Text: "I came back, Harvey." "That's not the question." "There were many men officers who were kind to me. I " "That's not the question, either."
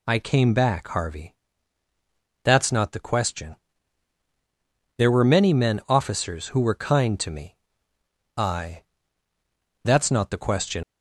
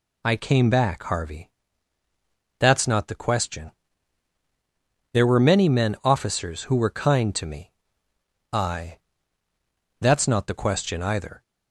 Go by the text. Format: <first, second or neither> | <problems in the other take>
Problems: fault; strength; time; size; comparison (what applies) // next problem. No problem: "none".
second | stops before "either"; at 10.8 s